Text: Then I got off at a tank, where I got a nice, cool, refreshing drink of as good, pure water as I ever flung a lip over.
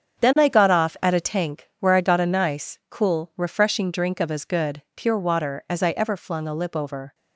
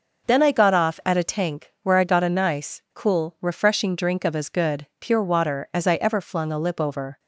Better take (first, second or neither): second